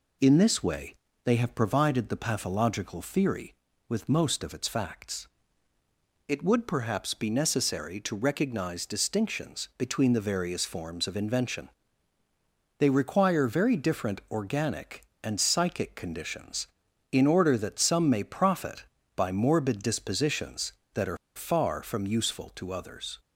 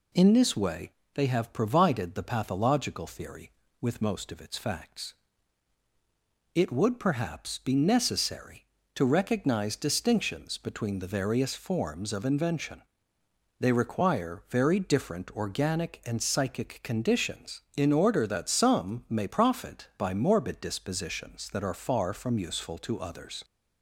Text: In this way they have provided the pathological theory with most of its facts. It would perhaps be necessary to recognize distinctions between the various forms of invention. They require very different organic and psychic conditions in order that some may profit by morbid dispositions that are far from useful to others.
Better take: second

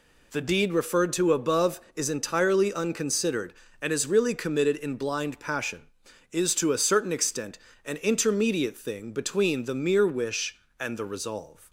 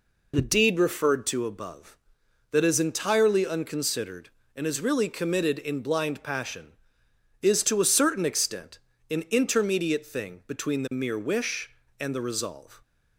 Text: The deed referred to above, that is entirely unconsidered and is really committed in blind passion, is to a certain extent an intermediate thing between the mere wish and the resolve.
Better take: second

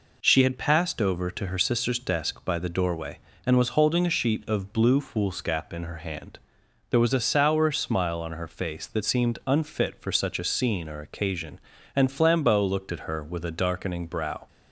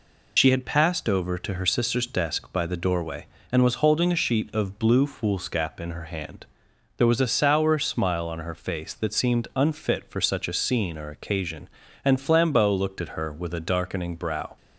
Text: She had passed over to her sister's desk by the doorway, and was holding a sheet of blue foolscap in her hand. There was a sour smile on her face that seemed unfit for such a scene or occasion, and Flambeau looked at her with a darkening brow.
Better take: first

